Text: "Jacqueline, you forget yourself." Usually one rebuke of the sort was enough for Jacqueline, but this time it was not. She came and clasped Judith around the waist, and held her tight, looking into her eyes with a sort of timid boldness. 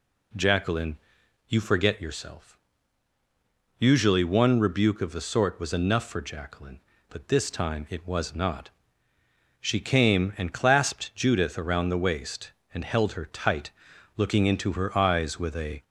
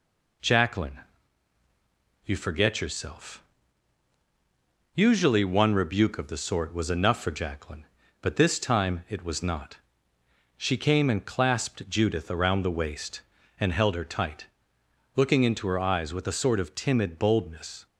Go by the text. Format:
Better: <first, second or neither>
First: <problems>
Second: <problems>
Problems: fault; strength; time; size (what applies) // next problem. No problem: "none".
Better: second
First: stops before "sort of timid boldness"; at 15.8 s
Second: none